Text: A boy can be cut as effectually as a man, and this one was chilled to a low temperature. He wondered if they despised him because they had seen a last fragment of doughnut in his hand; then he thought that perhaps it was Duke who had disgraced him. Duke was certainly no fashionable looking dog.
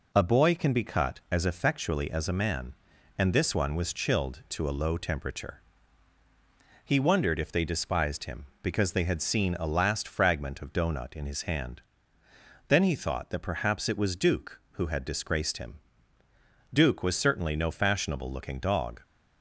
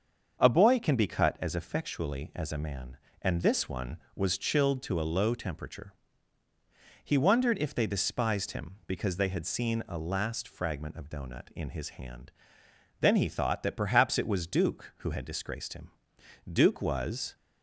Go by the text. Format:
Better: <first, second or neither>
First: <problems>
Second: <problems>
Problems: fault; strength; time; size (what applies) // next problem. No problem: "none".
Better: first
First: none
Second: starts louder than the rest; until 1.4 s; 7 dB // stops before "certainly no fashionable looking dog"; at 17.3 s